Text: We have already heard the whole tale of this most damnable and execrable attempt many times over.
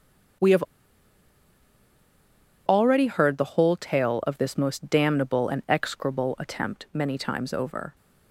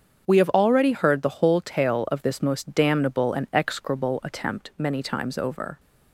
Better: second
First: starts louder than the rest; strong; until 3.4 s; 7.5 dB // pauses between "have" and "already"; strong; at 0.6 s; 2.0 s long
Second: starts louder than the rest; strong; until 1.3 s; 7.5 dB

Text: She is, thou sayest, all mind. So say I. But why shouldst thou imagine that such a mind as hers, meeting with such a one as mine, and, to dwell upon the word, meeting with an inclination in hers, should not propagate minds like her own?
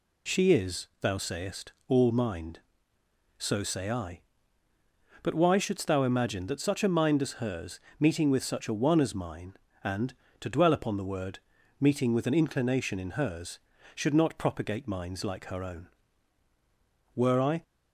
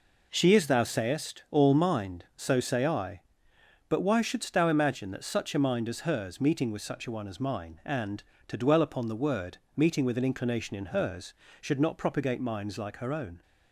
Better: second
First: goes on to say "Were I"; slight; from 17.1 s on; 0.48 s long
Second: none

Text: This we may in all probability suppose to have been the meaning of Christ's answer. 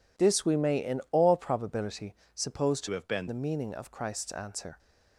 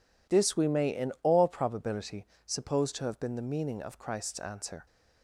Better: second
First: pauses between "probability" and "suppose"; slight; at 2.1 s; 0.20 s long // changes voice from "have" to "been"; from 2.9 to 3.2 s; 0.3 s long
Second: pauses between "probability" and "suppose"; slight; at 2.2 s; 0.20 s long

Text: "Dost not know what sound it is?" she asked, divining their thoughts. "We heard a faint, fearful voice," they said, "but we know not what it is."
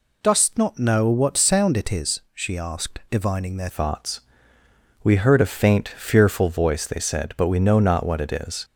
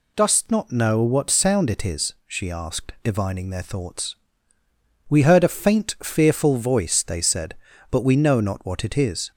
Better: second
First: changes voice at "thoughts"; from 3.6 s on; 5.0 s long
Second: none

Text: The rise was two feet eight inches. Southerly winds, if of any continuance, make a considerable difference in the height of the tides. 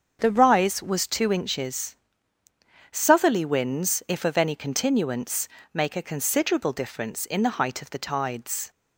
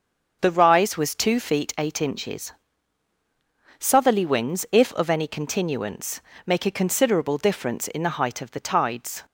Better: second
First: starts louder than the rest; until 1.2 s; 7 dB // skips "feet eight"; at 1.3 s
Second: starts louder than the rest; until 1.4 s; 6.5 dB

